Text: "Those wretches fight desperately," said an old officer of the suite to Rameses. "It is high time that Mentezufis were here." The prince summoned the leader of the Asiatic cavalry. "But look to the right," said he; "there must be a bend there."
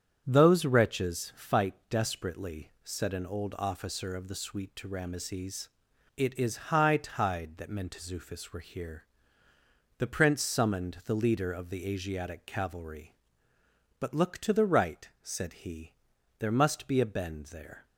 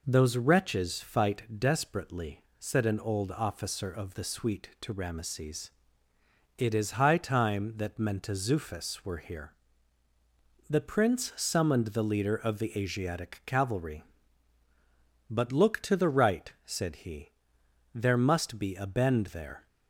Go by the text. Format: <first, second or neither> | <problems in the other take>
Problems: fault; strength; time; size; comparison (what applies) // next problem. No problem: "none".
second | starts louder than the rest; strong; until 1.2 s; 8.5 dB // pauses between "fight" and "desperately"; slight; at 1.7 s; 0.16 s long; slight in the second // says "tide" for "time"; at 6.9 s